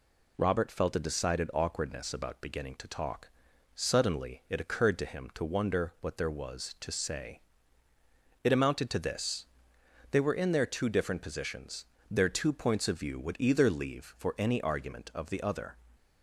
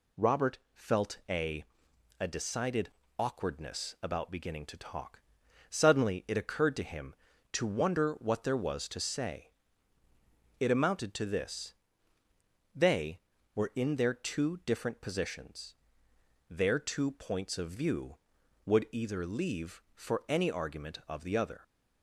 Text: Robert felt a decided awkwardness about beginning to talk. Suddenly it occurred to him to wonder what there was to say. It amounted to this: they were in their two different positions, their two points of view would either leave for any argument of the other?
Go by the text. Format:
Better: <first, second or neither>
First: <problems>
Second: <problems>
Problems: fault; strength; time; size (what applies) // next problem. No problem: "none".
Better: first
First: none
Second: pauses between "Robert" and "felt"; slight; at 0.5 s; 0.16 s long // says "a" twice; at 2.1 s // pauses between "decided" and "awkwardness"; slight; at 2.9 s; 0.28 s long